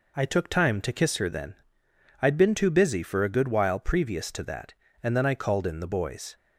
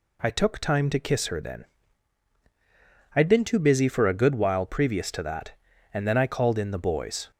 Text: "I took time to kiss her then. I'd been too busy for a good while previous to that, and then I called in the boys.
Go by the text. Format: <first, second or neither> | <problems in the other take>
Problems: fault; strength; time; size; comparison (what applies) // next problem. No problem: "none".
neither | none